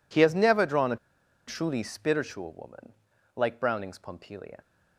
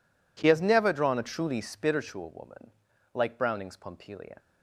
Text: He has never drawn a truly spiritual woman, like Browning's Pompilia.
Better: second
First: pauses between "a" and "truly"; noticeable; at 0.9 s; 0.51 s long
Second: none

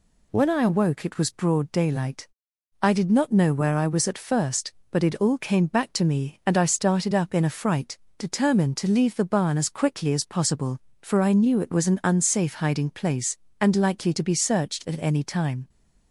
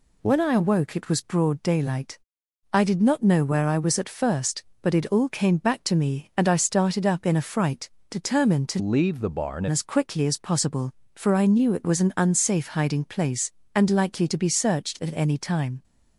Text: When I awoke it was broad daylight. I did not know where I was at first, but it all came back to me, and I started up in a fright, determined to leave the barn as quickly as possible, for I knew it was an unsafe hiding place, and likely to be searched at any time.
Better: first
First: none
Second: changes voice from "leave" to "barn"; from 8.7 to 9.6 s; 0.9 s long

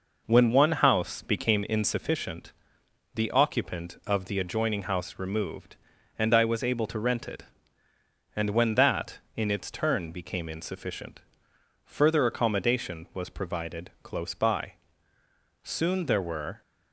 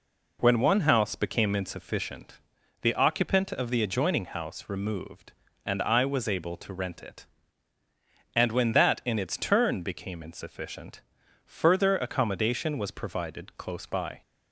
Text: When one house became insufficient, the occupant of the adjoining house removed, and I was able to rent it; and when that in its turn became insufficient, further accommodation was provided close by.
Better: second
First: goes on to say "Soon there were"; noticeable; from 15.6 s on; 1.0 s long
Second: none

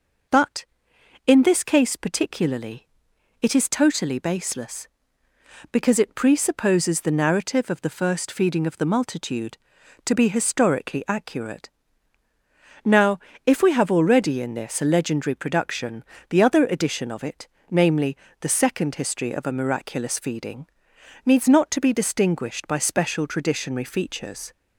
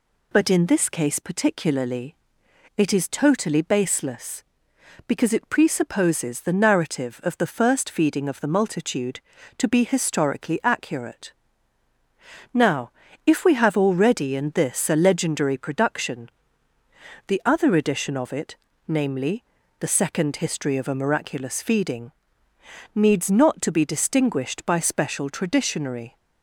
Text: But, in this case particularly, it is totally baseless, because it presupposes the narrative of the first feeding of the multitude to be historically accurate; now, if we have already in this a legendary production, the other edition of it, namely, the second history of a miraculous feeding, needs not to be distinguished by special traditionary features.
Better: first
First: none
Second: stops before "features"; at 26.1 s

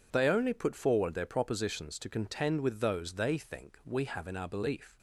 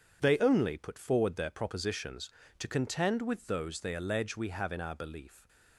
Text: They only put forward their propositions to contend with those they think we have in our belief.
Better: first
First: none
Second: says "allege" for "think"; at 3.9 s // stays silent after the last word; slight; from 5.2 s on; 0.5 s long

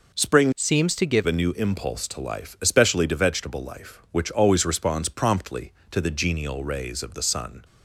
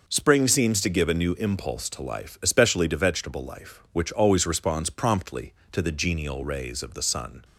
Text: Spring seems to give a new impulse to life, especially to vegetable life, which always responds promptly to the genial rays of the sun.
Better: second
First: changes voice from "seems" to "give"; from 0.5 to 1.2 s; 0.7 s long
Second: none

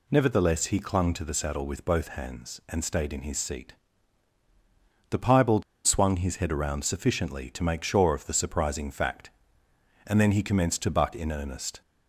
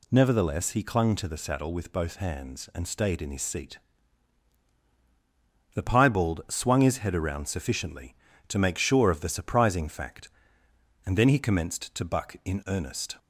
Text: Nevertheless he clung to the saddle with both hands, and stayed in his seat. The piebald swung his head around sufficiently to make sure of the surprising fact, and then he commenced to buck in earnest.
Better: second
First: pauses between "piebald" and "swung"; slight; at 5.6 s; 0.23 s long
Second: none

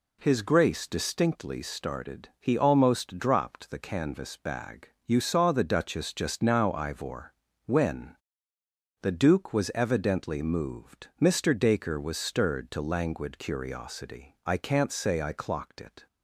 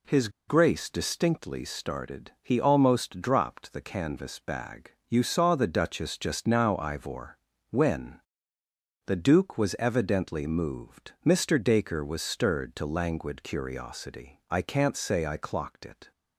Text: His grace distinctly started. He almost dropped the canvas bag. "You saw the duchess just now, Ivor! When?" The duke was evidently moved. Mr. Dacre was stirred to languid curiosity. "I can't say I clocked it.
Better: first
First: none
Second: pauses between "His" and "grace"; slight; at 0.2 s; 0.19 s long

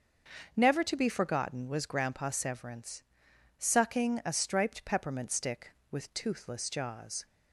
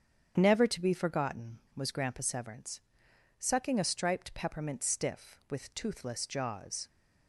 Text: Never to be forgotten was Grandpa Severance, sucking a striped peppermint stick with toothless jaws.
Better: first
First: starts louder than the rest; until 1.5 s; 6.5 dB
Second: starts louder than the rest; strong; until 1.3 s; 8.5 dB // says "stiff" for "stick"; at 4.8 s

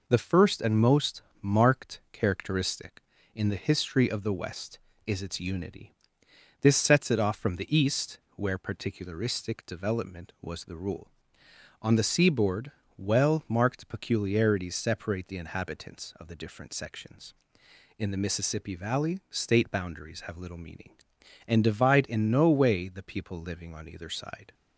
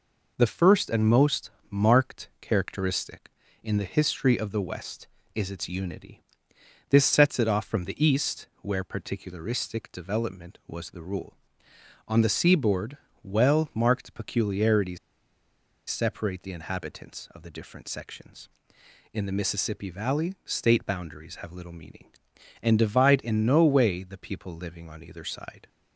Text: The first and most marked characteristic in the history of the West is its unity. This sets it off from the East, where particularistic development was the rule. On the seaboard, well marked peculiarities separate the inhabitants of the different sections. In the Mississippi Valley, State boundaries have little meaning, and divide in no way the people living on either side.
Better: first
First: pauses between "most" and "marked"; slight; at 1.2 s; 0.18 s long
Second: pauses between "most" and "marked"; slight; at 1.5 s; 0.18 s long // pauses between "peculiarities" and "separate"; noticeable; at 14.9 s; 0.92 s long

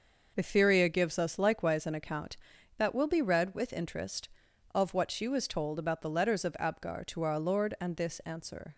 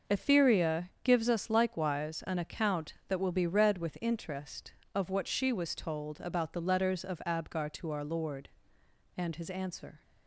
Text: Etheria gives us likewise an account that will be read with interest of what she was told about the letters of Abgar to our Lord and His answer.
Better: second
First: says "This" for "His"; at 7.9 s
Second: none

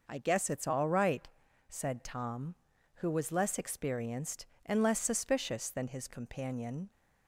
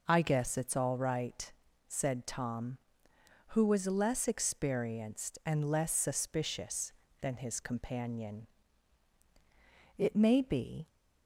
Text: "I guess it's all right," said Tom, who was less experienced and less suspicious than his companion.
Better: first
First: none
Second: goes on to say "It may be"; noticeable; from 9.9 s on; 0.90 s long

